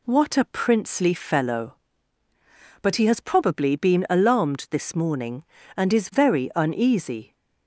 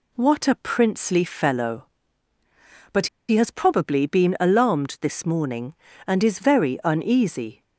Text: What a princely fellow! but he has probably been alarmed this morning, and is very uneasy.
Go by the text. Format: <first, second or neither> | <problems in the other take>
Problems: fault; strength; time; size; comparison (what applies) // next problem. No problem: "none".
first | pauses between "but" and "he"; slight; at 3.0 s; 0.21 s long